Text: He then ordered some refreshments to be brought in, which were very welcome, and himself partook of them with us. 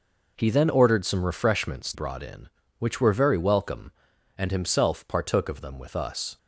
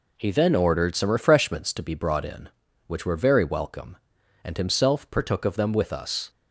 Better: second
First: skips "to be"; at 1.9 s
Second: none

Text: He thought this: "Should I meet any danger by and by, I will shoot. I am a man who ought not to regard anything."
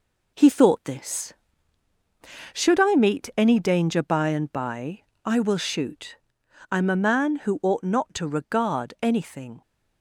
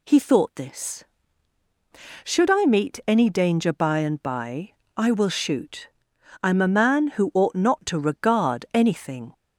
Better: second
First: gets quieter; noticeable; throughout; 5.5 dB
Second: none

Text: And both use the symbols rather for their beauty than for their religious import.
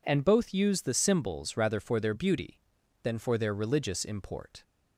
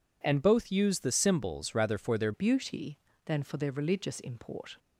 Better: first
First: none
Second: changes voice at "beauty"; from 2.3 s on; 2.4 s long

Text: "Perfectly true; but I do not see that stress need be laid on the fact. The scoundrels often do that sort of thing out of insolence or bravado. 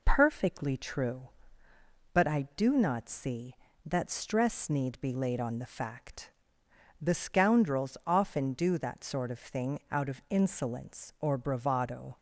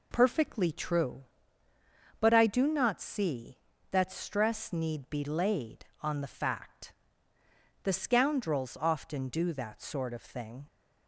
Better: first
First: none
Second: stops before "out of insolence or bravado"; at 10.6 s

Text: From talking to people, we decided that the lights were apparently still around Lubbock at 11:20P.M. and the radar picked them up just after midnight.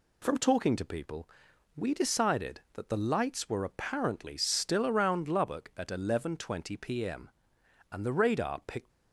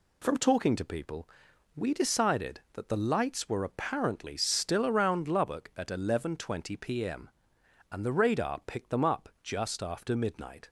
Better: second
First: stops before "them up just after midnight"; at 8.9 s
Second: none

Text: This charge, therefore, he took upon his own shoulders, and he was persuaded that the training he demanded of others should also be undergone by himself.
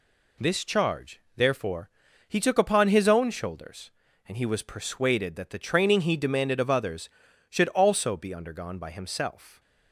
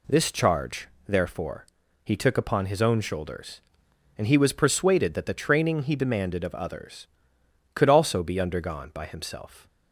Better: first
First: none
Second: says "could" for "should"; at 7.7 s

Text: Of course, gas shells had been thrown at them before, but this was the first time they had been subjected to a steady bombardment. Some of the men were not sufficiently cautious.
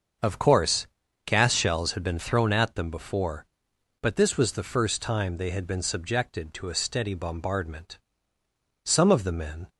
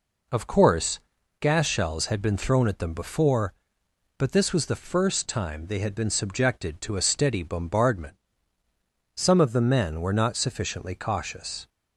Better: second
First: starts louder than the rest; until 1.5 s; 6.5 dB // stops before "were not sufficiently cautious"; at 9.6 s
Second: none

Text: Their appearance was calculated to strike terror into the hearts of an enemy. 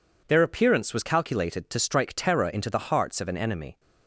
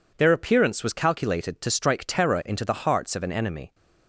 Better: neither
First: none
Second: none

